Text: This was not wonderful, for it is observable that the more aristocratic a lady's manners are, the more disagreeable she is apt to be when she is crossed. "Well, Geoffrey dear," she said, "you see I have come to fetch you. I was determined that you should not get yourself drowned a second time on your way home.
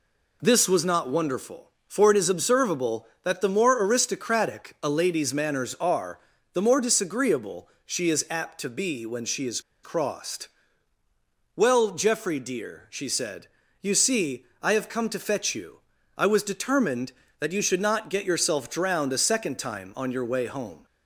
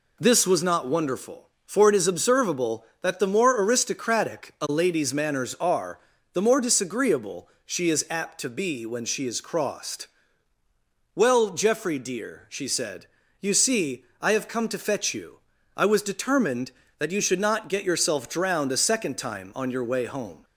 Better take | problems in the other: second | pauses between "disagreeable" and "she"; slight; at 7.6 s; 0.16 s long; slight in the second // pauses between "is" and "crossed"; slight; at 9.5 s; 0.23 s long // pauses between "see" and "I"; slight; at 14.4 s; 0.16 s long; slight in the second

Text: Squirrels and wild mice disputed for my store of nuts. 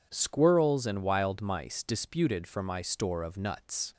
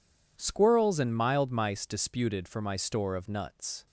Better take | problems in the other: first | says "mild" for "wild"; at 1.1 s

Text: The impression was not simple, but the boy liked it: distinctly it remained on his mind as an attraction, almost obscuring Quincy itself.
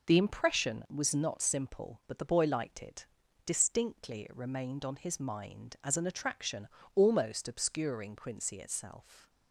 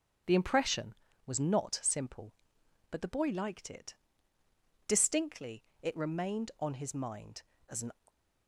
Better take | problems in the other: first | starts louder than the rest; strong; until 1.5 s; 7.5 dB // stops before "attraction almost obscuring Quincy itself"; at 8.0 s

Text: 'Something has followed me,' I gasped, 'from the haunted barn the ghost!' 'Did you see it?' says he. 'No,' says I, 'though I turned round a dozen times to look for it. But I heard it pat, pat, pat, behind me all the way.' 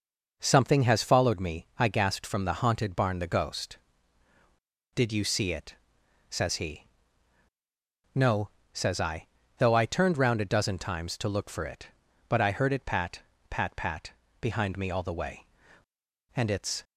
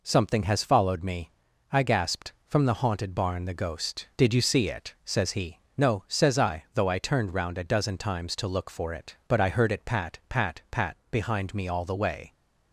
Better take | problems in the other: second | goes on to say "And it's"; slight; from 16.3 s on; 0.48 s long

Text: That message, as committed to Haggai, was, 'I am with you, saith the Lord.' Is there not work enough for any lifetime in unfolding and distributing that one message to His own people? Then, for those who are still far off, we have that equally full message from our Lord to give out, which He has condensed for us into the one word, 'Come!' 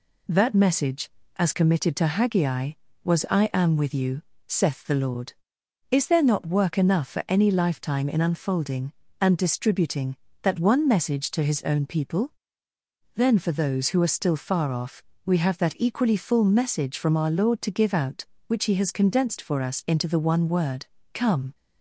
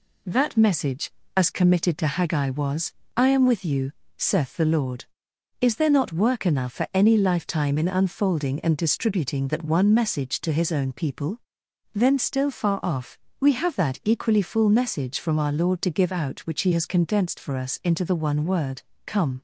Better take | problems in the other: first | skips "for those who are"; at 12.1 s

